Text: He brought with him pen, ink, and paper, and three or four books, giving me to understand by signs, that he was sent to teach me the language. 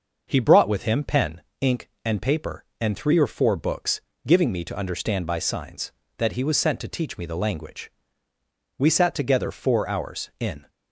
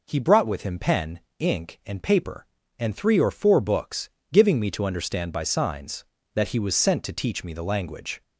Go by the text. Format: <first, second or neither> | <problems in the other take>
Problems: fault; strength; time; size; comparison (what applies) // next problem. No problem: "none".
second | starts louder than the rest; noticeable; until 1.2 s; 6 dB // goes on to say "We sat together four hours in"; strong; from 8.7 s on; 1.9 s long